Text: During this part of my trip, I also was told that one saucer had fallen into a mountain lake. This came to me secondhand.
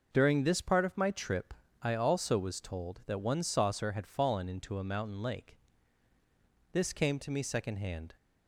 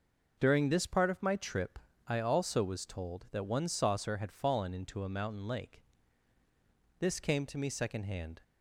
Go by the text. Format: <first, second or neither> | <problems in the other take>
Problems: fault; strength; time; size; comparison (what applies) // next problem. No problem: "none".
neither | none